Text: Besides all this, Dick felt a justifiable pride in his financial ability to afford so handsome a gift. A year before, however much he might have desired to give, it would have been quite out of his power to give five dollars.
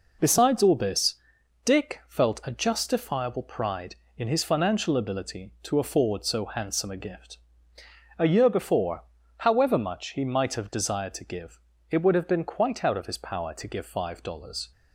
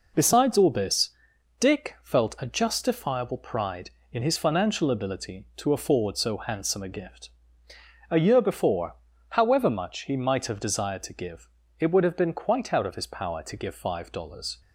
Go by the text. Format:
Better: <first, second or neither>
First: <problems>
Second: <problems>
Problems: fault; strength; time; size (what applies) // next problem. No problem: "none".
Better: neither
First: none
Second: none